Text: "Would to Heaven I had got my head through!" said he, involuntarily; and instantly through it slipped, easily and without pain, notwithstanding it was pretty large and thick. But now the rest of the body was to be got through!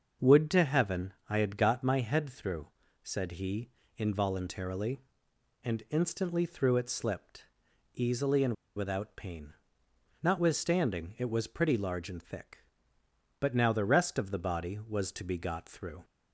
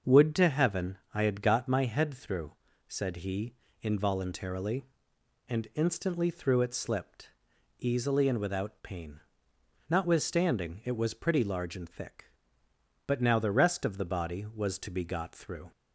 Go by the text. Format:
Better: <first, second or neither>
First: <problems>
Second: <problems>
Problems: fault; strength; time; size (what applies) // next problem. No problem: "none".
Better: second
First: starts louder than the rest; until 1.3 s; 6.5 dB // pauses between "Heaven" and "I"; slight; at 1.1 s; 0.16 s long // pauses between "and" and "without"; slight; at 8.5 s; 0.23 s long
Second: starts louder than the rest; until 1.2 s; 6.5 dB // pauses between "Heaven" and "I"; slight; at 0.9 s; 0.16 s long